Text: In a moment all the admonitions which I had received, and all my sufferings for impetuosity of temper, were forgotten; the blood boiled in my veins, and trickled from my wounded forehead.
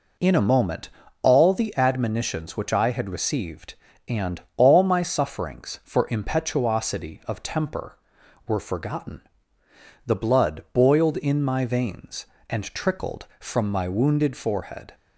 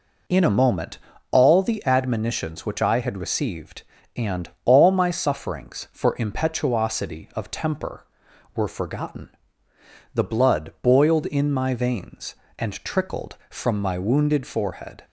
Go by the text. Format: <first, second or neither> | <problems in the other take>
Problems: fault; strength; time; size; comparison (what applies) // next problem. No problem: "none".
neither | pauses between "moment" and "all"; slight; the same in both // pauses between "and" and "all"; slight; the same in both